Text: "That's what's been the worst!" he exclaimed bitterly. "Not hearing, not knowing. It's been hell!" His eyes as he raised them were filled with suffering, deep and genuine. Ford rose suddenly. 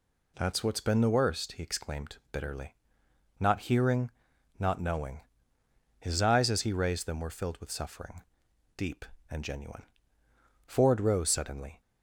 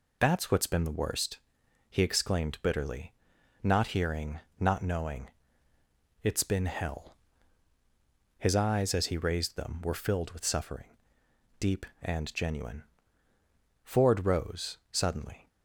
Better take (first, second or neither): second